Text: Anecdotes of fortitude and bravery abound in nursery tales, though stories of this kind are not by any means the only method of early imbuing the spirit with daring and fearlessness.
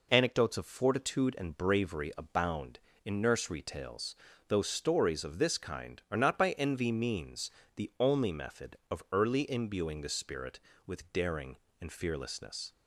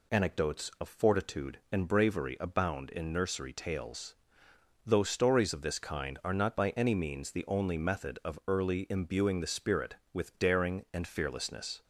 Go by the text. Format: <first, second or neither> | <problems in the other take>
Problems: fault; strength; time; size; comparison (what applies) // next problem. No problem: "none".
second | says "envy" for "any"; at 6.5 s // pauses between "means" and "the"; slight; at 7.5 s; 0.24 s long